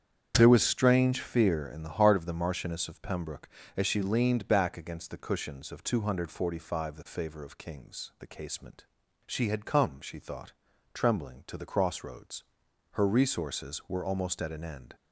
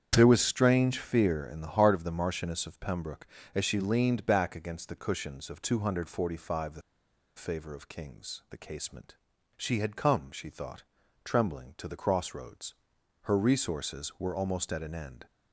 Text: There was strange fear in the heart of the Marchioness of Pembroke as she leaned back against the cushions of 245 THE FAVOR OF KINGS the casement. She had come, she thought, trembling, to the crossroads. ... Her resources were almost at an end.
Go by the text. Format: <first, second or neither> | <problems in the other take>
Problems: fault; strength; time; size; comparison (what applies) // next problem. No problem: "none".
first | starts louder than the rest; strong; until 1.1 s; 8 dB; strong in the first // pauses between "THE" and "FAVOR"; noticeable; at 6.8 s; 0.55 s long